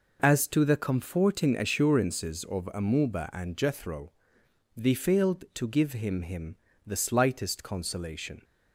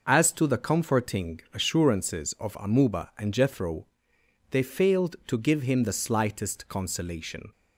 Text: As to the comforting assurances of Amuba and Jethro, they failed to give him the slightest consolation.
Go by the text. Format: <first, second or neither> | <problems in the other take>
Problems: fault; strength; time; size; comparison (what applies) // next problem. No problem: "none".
second | says "him" twice; at 6.2 s